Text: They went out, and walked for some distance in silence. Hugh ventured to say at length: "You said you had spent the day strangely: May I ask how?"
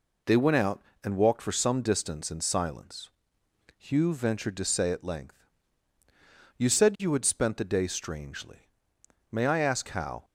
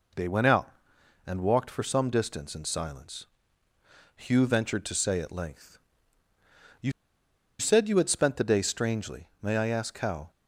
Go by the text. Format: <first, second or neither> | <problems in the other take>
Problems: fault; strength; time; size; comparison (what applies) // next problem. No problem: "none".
first | pauses between "You" and "said"; noticeable; at 6.9 s; 0.68 s long